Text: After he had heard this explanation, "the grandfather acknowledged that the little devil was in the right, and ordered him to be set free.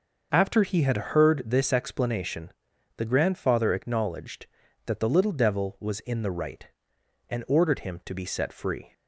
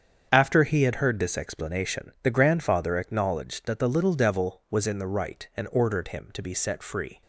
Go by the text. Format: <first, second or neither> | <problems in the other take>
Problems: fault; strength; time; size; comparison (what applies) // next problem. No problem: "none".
neither | starts louder than the rest; the same in both